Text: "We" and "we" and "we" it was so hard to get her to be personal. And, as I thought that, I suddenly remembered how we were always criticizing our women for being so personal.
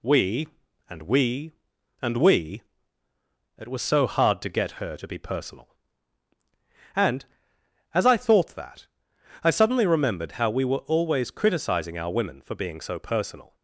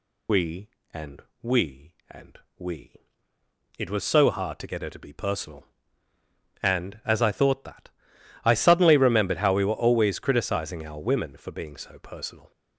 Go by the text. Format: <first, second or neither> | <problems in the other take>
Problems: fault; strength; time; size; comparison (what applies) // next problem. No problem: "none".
first | loses the start of "We"; at 0.2 s; 40 ms // pauses between "and" and "we"; slight; at 1.2 s; 0.18 s long // pauses between "and" and "we"; slight; at 2.3 s; 0.22 s long // pauses between "we" and "it"; noticeable; at 2.9 s; 0.88 s long; noticeable in the first